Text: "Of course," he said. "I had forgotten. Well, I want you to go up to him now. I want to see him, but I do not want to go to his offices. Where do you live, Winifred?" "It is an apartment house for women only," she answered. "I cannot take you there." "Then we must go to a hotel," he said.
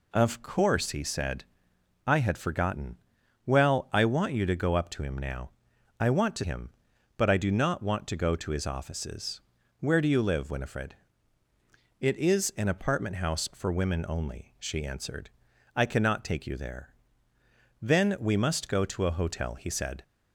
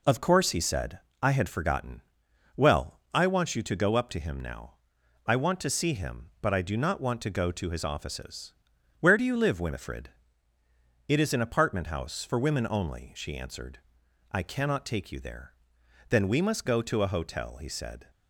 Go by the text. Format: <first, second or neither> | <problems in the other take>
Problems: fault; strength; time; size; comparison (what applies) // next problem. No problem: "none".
second | skips "see"; at 6.4 s